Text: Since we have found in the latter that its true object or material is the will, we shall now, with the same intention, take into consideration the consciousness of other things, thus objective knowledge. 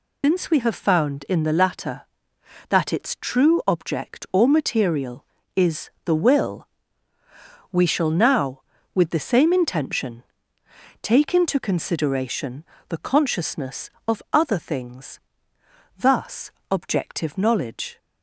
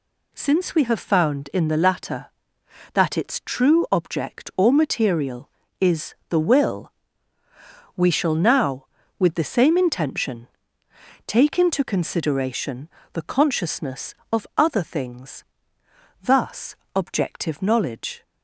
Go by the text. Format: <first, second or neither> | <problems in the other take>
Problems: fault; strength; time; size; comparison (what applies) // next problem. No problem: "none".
second | loses the start of "Since"; at 0.2 s; 140 ms // pauses between "consideration" and "the"; slight; at 12.6 s; 0.24 s long; slight in the second // pauses between "thus" and "objective"; slight; at 16.4 s; 0.20 s long; slight in the second